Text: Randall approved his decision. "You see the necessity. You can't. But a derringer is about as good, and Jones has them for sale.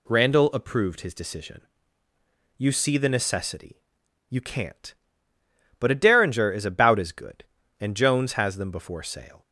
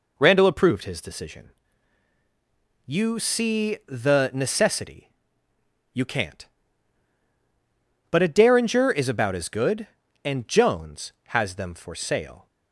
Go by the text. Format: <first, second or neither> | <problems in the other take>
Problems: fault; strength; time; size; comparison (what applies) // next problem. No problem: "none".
second | says "before" for "for"; at 8.6 s